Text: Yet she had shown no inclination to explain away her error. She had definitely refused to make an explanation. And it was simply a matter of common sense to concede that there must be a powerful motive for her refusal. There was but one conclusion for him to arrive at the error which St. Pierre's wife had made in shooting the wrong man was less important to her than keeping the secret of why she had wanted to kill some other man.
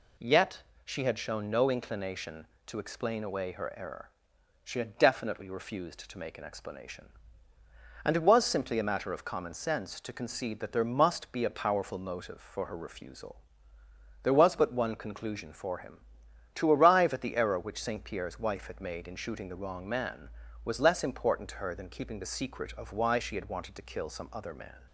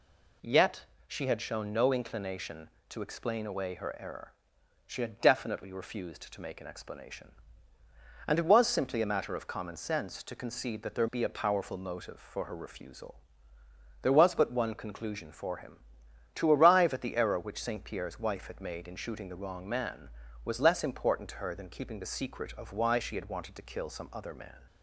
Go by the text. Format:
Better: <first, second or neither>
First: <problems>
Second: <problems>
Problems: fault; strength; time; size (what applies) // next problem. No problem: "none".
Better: first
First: pauses between "Yet" and "she"; slight; at 0.6 s; 0.20 s long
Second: pauses between "Yet" and "she"; slight; at 0.8 s; 0.20 s long // skips "must"; at 11.0 s